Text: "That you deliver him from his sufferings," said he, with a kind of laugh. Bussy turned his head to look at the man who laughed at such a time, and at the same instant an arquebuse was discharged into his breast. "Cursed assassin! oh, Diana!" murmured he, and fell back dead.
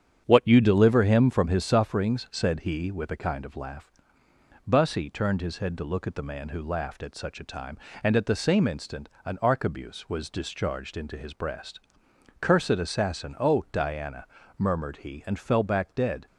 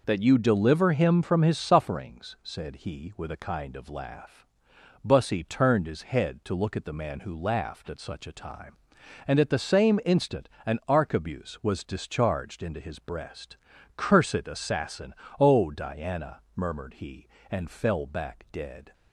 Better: second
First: starts louder than the rest; strong; until 1.2 s; 8.5 dB // says "What" for "That"; at 0.2 s // pauses between "instant" and "an"; slight; at 9.0 s; 0.16 s long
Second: pauses between "instant" and "an"; slight; at 10.4 s; 0.20 s long

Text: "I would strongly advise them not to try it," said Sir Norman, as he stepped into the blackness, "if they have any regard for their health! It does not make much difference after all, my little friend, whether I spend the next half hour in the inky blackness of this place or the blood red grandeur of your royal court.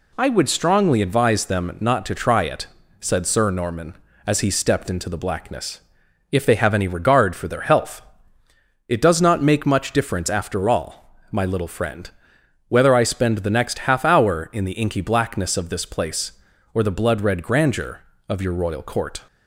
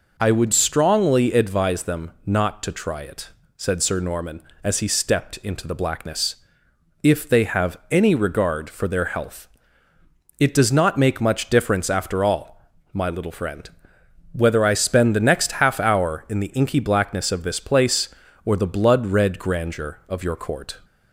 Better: first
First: none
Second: skips "royal"; at 20.3 s

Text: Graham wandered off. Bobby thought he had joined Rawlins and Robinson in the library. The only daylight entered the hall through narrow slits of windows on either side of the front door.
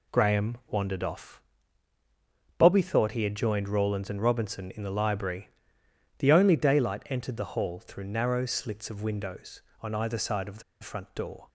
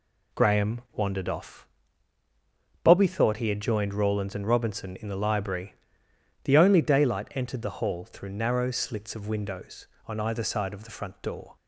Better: second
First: pauses between "the" and "front"; slight; at 10.6 s; 0.21 s long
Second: none

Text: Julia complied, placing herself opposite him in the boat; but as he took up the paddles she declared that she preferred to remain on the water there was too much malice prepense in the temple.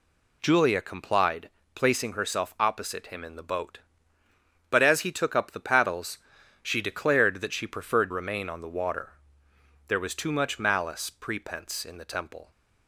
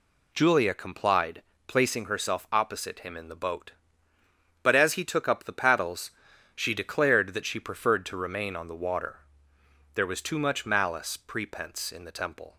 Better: second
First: pauses between "paddles" and "she"; noticeable; at 6.1 s; 0.46 s long // skips "to"; at 8.1 s // pauses between "water" and "there"; noticeable; at 9.1 s; 0.76 s long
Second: pauses between "paddles" and "she"; noticeable; at 6.0 s; 0.46 s long // pauses between "water" and "there"; noticeable; at 9.1 s; 0.76 s long

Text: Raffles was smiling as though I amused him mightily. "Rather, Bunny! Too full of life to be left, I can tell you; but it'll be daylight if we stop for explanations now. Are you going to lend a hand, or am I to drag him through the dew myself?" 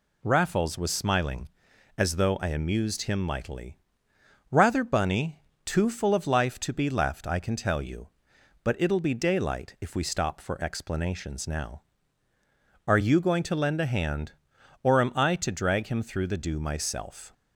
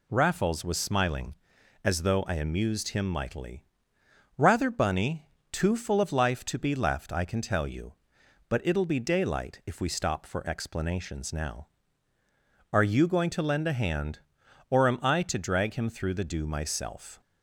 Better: neither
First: none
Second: none

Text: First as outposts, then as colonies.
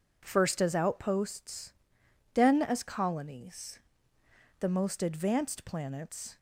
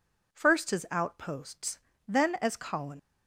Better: second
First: goes on to say "The most advanced planets"; strong; from 4.5 s on; 1.7 s long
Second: none

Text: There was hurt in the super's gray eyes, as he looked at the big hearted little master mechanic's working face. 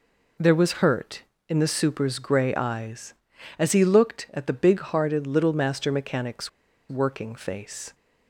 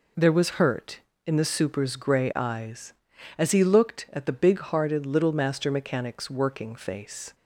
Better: second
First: pauses between "mechanic's" and "working"; at 6.4 s; 0.40 s long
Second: none

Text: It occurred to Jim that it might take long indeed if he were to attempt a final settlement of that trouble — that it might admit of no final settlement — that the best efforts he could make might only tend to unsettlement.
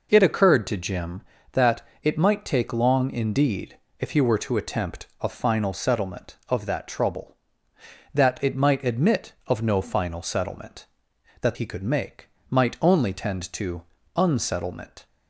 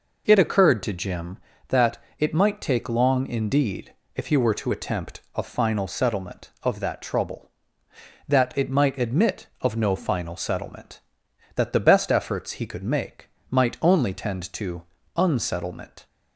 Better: second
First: pauses between "that" and "it"; slight; at 1.8 s; 0.20 s long // pauses between "indeed" and "if"; slight; at 3.7 s; 0.22 s long // skips "the best efforts"; at 11.5 s // pauses between "make" and "might"; slight; at 12.2 s; 0.22 s long // pauses between "to" and "unsettlement"; slight; at 13.8 s; 0.34 s long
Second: pauses between "that" and "it"; slight; at 1.9 s; 0.20 s long // pauses between "indeed" and "if"; slight; at 3.9 s; 0.22 s long // pauses between "make" and "might"; slight; at 13.2 s; 0.22 s long // pauses between "to" and "unsettlement"; slight; at 14.8 s; 0.34 s long

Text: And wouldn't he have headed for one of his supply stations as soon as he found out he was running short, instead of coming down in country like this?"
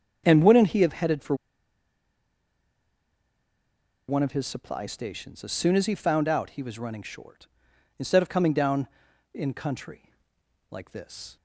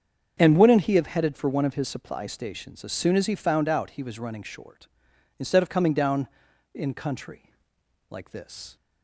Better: second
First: starts louder than the rest; strong; until 1.2 s; 7 dB // pauses between "for" and "one"; strong; at 1.3 s; 2.7 s long // pauses between "country" and "like"; noticeable; at 10.1 s; 0.58 s long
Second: starts louder than the rest; strong; until 1.3 s; 7 dB // pauses between "country" and "like"; noticeable; at 7.5 s; 0.57 s long

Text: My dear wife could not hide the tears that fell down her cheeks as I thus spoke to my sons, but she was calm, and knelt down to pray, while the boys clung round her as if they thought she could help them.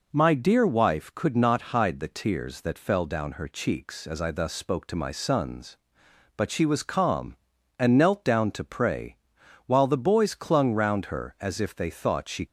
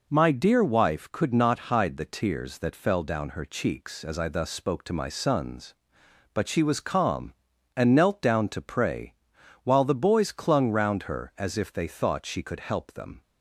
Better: second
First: stops before "could help them"; at 12.4 s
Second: none

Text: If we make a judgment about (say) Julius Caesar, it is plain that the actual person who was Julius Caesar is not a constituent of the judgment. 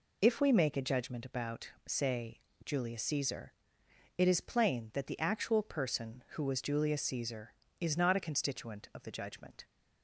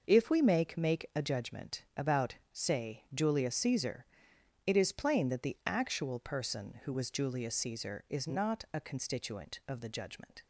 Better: first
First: none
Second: starts louder than the rest; noticeable; until 1.1 s; 6 dB // says "make" twice; at 0.7 s

